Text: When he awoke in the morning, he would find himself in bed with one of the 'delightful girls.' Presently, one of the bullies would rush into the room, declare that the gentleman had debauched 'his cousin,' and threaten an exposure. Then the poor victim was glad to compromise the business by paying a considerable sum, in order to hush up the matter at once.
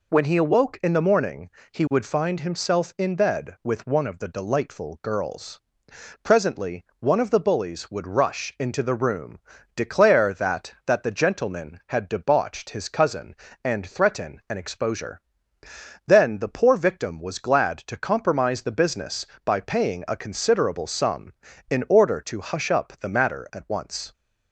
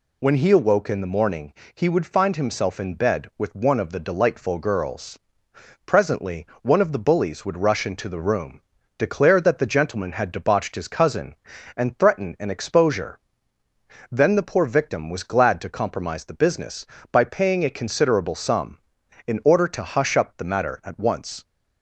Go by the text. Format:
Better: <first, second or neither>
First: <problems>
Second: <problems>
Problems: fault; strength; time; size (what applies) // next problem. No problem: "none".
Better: second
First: says "that" twice; at 10.8 s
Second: none